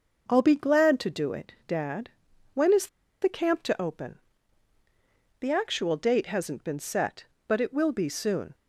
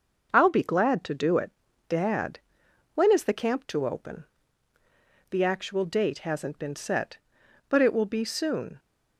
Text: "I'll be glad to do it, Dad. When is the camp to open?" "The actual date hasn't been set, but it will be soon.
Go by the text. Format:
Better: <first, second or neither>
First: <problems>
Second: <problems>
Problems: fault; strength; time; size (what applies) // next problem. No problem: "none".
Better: second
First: pauses between "is" and "the"; slight; at 2.8 s; 0.34 s long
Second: none